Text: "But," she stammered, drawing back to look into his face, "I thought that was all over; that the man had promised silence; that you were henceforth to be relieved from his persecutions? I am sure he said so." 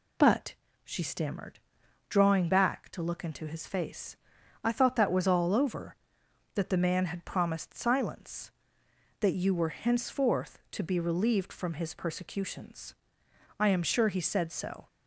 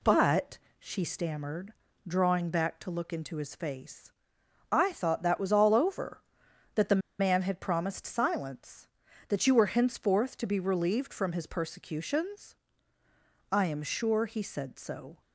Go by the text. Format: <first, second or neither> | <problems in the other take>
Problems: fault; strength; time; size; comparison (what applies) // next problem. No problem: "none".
first | pauses between "the" and "man"; slight; at 6.9 s; 0.21 s long